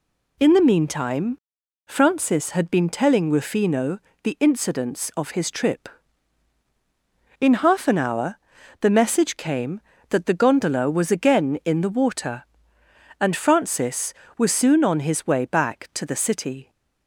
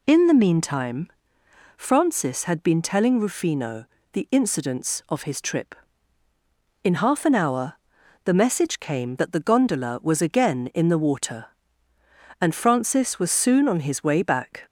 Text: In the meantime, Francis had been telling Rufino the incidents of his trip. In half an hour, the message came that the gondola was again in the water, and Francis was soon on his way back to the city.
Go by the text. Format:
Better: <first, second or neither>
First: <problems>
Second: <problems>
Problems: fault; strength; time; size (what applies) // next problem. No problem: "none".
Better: first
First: pauses between "Rufino" and "the"; slight; at 3.9 s; 0.24 s long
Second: pauses between "Rufino" and "the"; slight; at 3.8 s; 0.26 s long // stops before "to the city"; at 14.6 s